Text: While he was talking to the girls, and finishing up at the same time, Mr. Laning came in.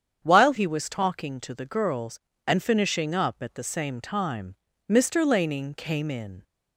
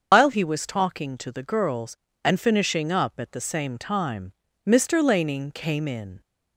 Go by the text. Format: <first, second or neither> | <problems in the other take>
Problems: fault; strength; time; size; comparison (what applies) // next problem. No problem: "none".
first | loses the start of "While"; at 0.1 s; 115 ms // starts louder than the rest; until 1.1 s; 7 dB; strong in the first